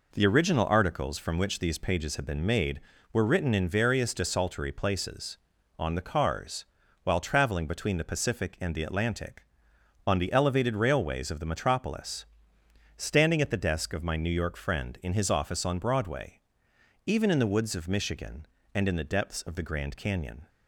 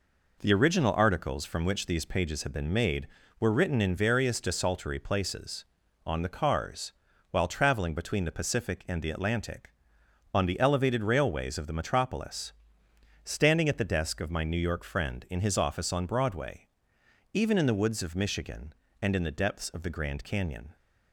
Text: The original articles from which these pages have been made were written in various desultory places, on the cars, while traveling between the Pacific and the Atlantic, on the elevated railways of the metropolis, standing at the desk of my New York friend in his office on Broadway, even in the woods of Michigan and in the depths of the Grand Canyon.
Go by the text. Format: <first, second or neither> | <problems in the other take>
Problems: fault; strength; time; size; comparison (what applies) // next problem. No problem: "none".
neither | none